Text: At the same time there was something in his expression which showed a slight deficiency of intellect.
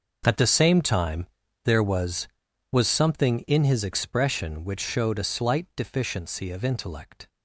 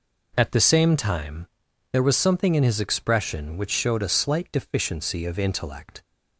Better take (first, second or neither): second